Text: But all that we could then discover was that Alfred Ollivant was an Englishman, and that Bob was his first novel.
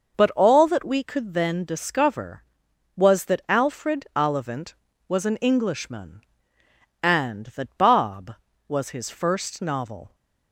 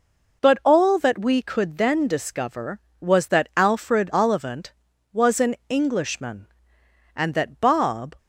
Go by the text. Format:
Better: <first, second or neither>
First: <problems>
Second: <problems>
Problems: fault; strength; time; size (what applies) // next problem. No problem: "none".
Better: first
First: none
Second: stops before "was his first novel"; at 8.1 s